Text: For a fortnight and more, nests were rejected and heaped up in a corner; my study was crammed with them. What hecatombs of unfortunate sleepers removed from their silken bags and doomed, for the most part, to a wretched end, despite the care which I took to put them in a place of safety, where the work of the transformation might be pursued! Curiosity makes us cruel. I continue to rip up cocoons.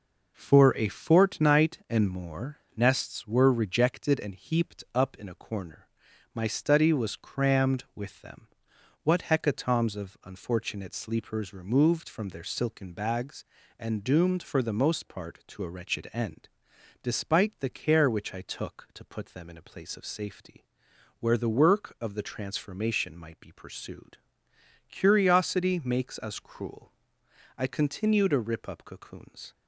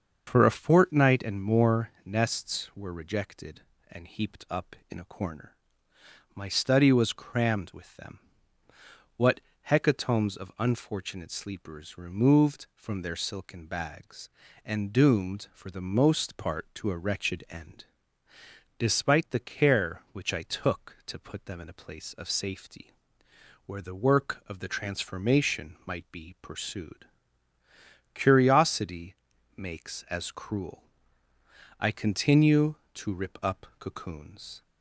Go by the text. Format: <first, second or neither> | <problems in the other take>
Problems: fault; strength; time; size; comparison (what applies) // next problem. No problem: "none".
first | starts louder than the rest; until 1.2 s; 6.5 dB // pauses between "What" and "hecatombs"; slight; at 9.4 s; 0.30 s long // pauses between "Curiosity" and "makes"; noticeable; at 29.1 s; 0.46 s long // says "as" for "us"; at 30.0 s